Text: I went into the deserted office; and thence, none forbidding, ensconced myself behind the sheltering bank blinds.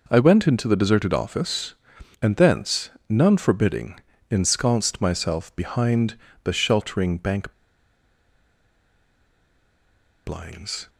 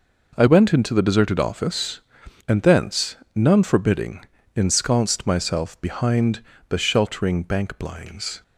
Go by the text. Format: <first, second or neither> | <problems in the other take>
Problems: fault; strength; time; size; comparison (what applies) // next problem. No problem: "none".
second | pauses between "behind" and "the"; slight; at 6.1 s; 0.28 s long; slight in the second // pauses between "bank" and "blinds"; strong; at 7.5 s; 2.7 s long